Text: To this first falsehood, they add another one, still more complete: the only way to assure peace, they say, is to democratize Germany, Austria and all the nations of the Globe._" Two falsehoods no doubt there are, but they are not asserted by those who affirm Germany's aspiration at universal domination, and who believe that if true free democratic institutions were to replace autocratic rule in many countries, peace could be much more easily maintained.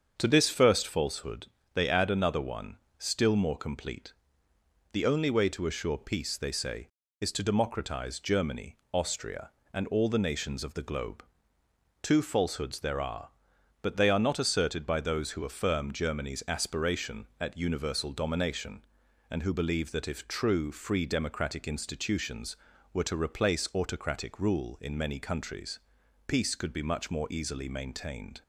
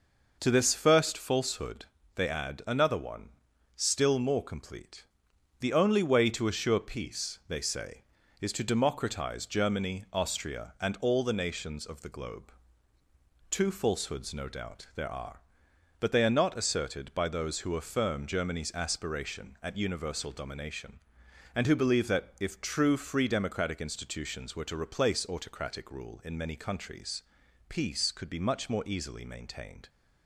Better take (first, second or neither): second